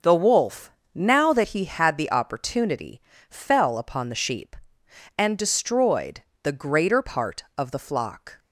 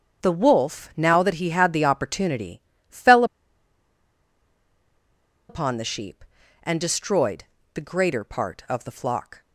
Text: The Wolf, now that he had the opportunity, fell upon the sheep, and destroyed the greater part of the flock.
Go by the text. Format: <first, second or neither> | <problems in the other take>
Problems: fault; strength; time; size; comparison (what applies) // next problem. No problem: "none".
first | starts louder than the rest; strong; until 1.2 s; 7.5 dB // pauses between "fell" and "upon"; strong; at 3.2 s; 2.2 s long // pauses between "destroyed" and "the"; slight; at 7.4 s; 0.30 s long; slight in the first